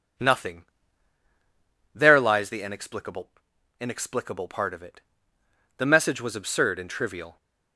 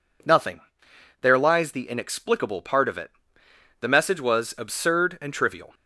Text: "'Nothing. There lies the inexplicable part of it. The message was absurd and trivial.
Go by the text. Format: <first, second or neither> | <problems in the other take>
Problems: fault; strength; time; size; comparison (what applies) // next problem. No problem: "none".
second | says "inexplicable" twice; at 3.7 s